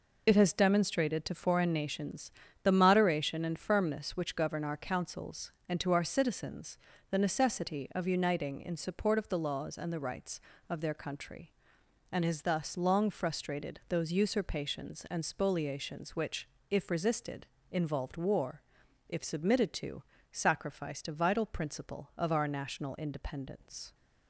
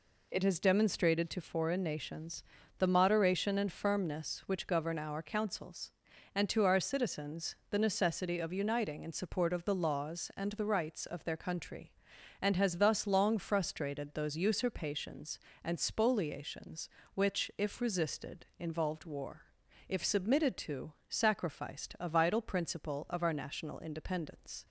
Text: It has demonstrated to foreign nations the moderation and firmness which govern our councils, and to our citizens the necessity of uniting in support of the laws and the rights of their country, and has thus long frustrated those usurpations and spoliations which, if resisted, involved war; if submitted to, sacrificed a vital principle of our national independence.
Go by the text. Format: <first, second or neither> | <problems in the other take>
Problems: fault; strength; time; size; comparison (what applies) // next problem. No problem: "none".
second | loses the start of "It"; at 0.2 s; 55 ms // pauses between "nations" and "the"; slight; at 2.3 s; 0.32 s long; slight in the second // pauses between "citizens" and "the"; slight; at 6.7 s; 0.34 s long; slight in the second